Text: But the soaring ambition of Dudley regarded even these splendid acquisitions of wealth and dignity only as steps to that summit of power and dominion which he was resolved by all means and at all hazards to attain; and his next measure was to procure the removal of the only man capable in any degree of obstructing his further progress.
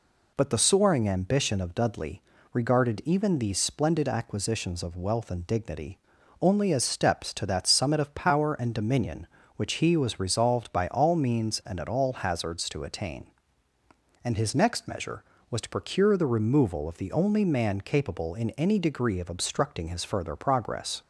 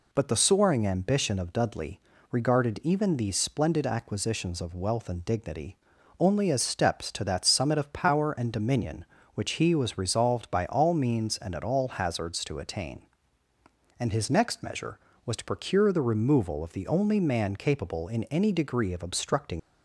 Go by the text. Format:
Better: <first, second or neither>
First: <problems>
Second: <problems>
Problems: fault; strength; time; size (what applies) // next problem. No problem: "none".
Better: first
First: pauses between "Dudley" and "regarded"; slight; at 2.2 s; 0.32 s long // pauses between "dignity" and "only"; at 5.9 s; 0.42 s long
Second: pauses between "Dudley" and "regarded"; slight; at 1.9 s; 0.32 s long // pauses between "dignity" and "only"; at 5.7 s; 0.42 s long // stops before "his further progress"; at 19.5 s